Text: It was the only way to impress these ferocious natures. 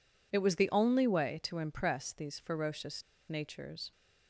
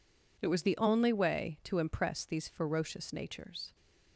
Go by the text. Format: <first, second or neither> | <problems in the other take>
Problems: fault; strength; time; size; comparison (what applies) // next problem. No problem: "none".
second | pauses between "ferocious" and "natures"; slight; at 3.0 s; 0.25 s long